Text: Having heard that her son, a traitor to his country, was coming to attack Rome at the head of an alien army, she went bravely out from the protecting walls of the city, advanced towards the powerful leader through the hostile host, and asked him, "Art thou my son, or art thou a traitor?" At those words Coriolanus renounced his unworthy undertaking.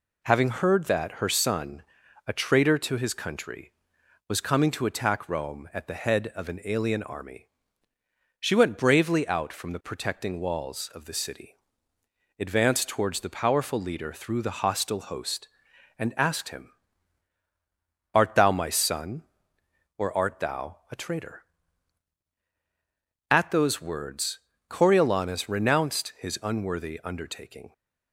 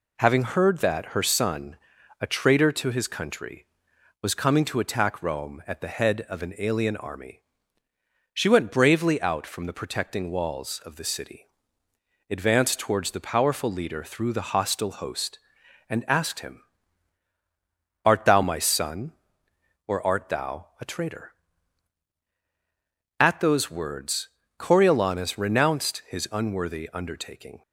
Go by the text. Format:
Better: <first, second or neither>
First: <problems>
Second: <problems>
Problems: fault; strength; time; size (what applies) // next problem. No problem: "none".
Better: neither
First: pauses between "words" and "Coriolanus"; slight; at 24.3 s; 0.30 s long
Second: pauses between "words" and "Coriolanus"; slight; at 24.2 s; 0.30 s long